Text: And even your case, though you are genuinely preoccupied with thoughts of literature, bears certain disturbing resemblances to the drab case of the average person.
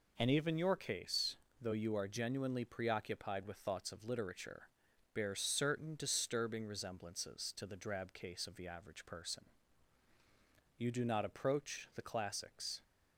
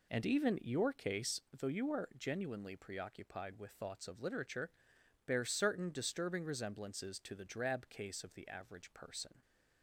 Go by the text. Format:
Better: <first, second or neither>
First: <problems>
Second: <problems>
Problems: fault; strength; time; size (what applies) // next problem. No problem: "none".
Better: second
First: goes on to say "You do not approach the classics"; strong; from 10.7 s on; 2.0 s long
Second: none